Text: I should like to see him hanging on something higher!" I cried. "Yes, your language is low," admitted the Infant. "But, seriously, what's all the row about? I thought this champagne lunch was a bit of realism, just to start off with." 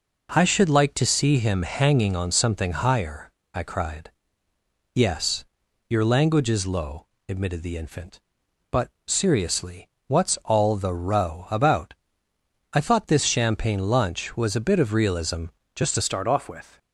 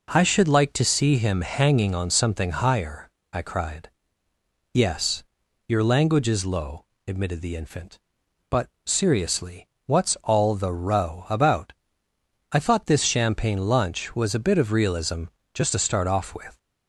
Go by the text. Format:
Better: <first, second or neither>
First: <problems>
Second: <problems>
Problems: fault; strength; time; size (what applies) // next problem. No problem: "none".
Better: second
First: changes voice at "start"; from 16.0 s on; 0.7 s long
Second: none